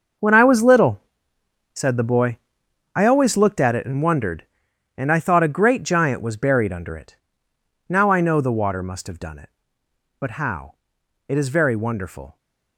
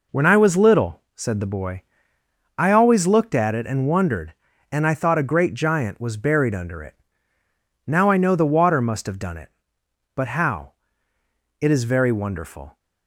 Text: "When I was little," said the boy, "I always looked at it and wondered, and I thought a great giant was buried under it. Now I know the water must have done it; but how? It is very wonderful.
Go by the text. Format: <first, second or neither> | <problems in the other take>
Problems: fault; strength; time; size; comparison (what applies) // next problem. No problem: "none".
second | gets quieter; strong; throughout; 12.5 dB